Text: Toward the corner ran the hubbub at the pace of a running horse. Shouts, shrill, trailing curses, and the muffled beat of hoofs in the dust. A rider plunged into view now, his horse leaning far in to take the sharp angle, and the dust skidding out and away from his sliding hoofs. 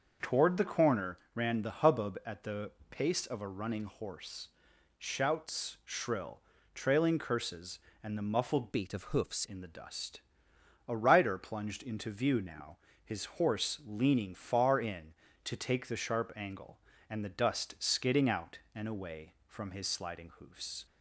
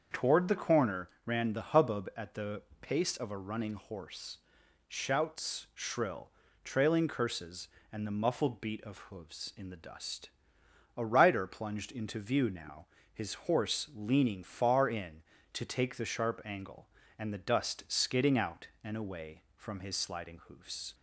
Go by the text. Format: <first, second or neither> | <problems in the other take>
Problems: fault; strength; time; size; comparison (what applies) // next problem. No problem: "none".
second | starts louder than the rest; until 1.3 s; 6.5 dB; also in the second // pauses between "corner" and "ran"; slight; at 1.1 s; 0.18 s long; slight in the second // pauses between "the" and "pace"; slight; at 2.7 s; 0.18 s long; slight in the second // changes voice from "beat" to "hoofs"; from 8.7 to 9.4 s; 0.7 s long